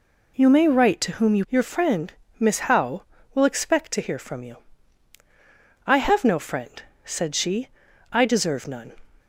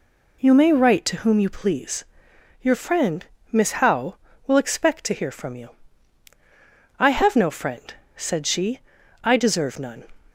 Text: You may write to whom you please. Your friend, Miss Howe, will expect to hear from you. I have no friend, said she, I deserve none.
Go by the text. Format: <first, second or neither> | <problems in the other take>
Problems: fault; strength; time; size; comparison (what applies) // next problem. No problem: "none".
second | skips "please"; at 1.4 s